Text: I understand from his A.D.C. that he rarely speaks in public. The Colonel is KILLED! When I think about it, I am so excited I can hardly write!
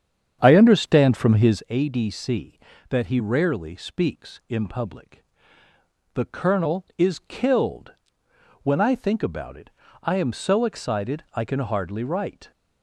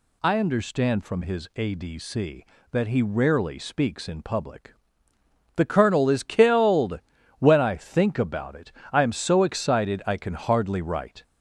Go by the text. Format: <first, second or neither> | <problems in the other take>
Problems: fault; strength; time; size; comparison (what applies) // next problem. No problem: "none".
second | starts louder than the rest; strong; until 1.6 s; 8 dB